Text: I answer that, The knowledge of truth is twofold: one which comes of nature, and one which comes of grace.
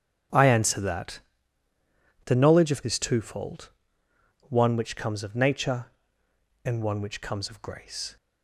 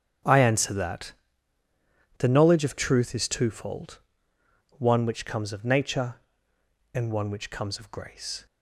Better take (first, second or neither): second